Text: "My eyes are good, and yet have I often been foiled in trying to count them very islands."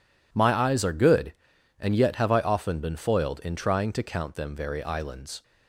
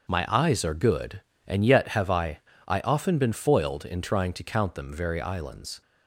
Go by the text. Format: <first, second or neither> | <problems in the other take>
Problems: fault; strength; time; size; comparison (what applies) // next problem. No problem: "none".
first | starts louder than the rest; until 1.1 s; 6 dB // says "I" twice; at 2.6 s